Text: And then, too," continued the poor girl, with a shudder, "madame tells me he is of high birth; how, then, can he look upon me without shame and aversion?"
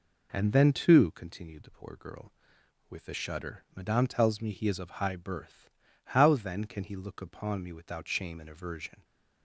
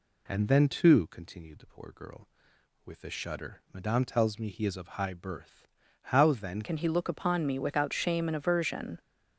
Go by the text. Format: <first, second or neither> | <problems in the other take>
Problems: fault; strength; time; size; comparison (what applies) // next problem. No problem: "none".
first | changes voice at "can"; from 6.6 s on; 2.3 s long